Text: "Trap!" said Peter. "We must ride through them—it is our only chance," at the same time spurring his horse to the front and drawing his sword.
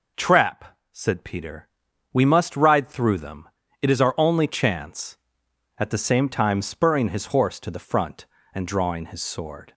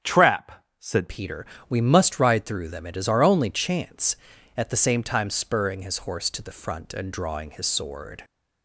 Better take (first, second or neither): first